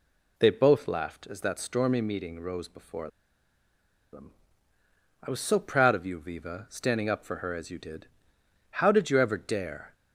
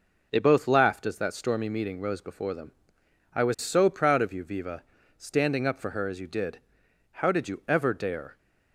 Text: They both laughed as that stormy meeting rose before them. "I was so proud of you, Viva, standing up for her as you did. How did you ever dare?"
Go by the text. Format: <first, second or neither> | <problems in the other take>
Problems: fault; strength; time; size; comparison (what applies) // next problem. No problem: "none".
second | pauses between "before" and "them"; at 3.0 s; 1.0 s long